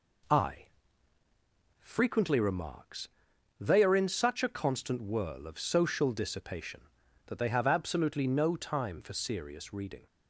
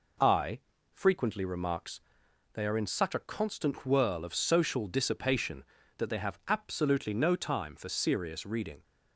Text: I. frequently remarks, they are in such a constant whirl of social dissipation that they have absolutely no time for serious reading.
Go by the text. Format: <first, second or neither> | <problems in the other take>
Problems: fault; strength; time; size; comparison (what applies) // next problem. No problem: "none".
neither | none